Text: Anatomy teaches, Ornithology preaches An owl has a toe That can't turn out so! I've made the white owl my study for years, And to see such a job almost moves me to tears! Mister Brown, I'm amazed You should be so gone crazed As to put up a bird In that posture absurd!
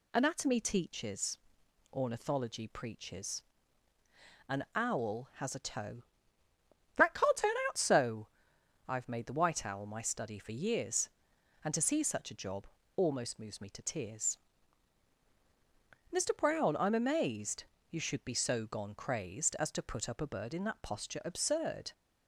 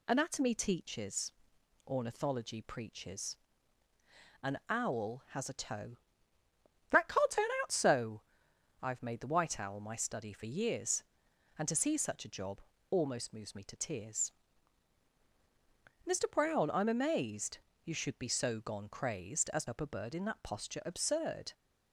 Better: first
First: pauses between "preaches" and "An"; at 3.4 s; 1.0 s long // pauses between "job" and "almost"; slight; at 12.6 s; 0.30 s long // pauses between "amazed" and "You"; slight; at 17.6 s; 0.26 s long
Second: pauses between "preaches" and "An"; at 3.3 s; 1.0 s long // pauses between "job" and "almost"; slight; at 12.5 s; 0.30 s long // pauses between "amazed" and "You"; slight; at 17.5 s; 0.26 s long // skips "to put"; at 19.6 s

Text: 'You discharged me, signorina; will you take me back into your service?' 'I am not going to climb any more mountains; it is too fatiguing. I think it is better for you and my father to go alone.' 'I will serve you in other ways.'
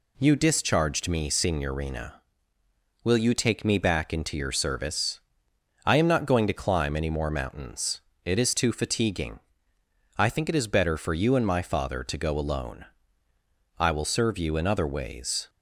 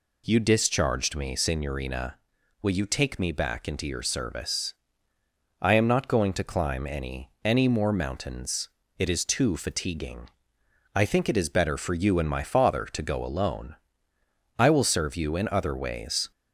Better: first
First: none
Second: says "any" twice; at 7.4 s

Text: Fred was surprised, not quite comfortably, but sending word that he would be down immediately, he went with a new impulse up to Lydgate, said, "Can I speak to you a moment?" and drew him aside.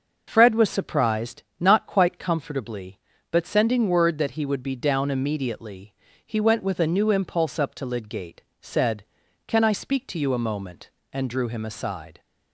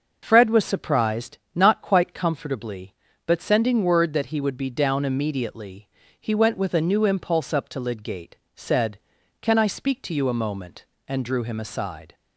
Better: neither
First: none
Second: none

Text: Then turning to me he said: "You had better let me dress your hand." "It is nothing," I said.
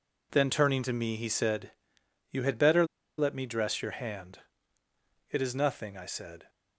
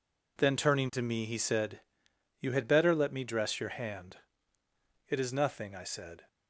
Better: second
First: pauses between "better" and "let"; slight; at 2.8 s; 0.32 s long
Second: none

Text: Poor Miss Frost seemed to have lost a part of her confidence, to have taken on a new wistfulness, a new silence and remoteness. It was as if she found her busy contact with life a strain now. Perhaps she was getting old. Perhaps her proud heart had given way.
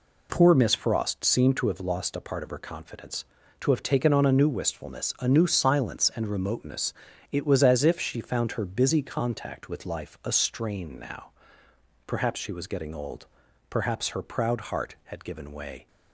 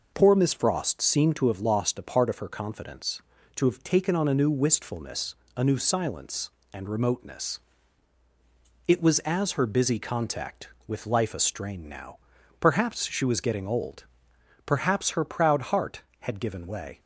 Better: first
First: none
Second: skips "if she found"; at 9.5 s

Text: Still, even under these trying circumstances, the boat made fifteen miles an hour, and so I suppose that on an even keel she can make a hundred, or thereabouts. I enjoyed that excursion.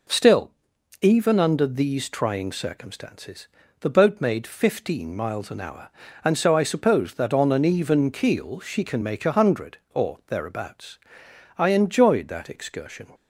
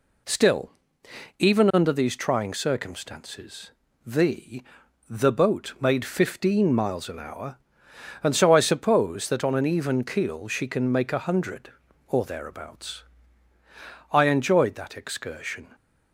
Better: first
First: none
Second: says "the" twice; at 5.0 s

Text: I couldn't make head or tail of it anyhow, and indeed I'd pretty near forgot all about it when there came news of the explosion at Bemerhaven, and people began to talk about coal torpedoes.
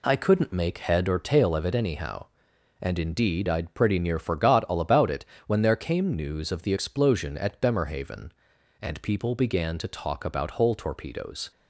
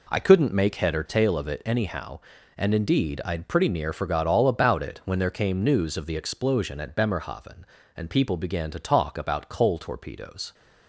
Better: second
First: pauses between "it" and "when"; slight; at 5.2 s; 0.22 s long // says "hole" for "coal"; at 10.5 s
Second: none

